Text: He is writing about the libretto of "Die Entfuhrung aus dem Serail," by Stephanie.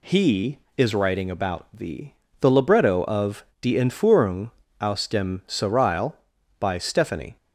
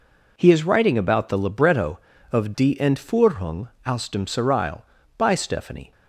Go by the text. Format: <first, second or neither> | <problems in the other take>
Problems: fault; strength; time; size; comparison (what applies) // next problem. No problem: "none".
second | says "the" twice; at 2.4 s // pauses between "of" and "Die"; slight; at 3.4 s; 0.16 s long // pauses between "Entfuhrung" and "aus"; slight; at 4.5 s; 0.30 s long; slight in the second